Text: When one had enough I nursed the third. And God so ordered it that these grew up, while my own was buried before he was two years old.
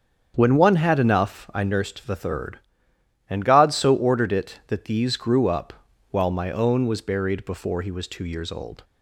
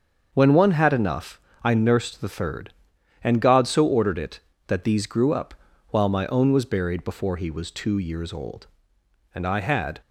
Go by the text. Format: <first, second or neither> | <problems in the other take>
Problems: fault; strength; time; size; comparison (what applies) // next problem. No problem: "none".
first | starts louder than the rest; until 1.3 s; 7 dB; strong in the first // pauses between "enough" and "I"; slight; at 1.3 s; 0.24 s long // goes on to say "And I had"; noticeable; from 9.3 s on; 0.68 s long